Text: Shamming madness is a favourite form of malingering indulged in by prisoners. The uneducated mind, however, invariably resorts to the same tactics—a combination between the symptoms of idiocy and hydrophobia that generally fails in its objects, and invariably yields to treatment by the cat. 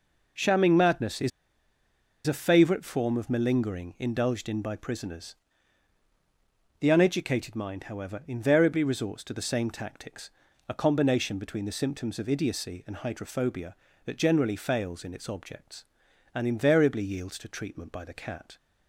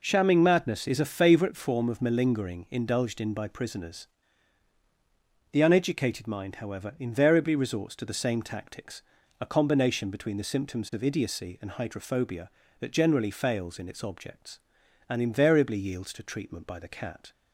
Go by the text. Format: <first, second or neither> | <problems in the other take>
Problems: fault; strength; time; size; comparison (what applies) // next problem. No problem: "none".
second | pauses between "is" and "a"; noticeable; at 1.3 s; 0.96 s long